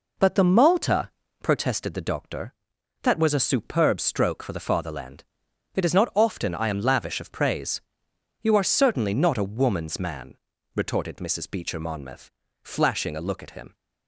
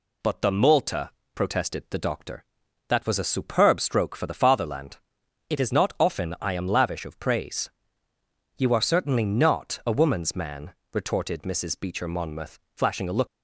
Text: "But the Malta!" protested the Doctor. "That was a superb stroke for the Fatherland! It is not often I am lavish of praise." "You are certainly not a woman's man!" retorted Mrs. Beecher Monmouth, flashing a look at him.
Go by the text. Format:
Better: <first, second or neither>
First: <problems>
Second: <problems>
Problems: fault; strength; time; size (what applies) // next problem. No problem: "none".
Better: first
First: none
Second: stops before "at him"; at 13.2 s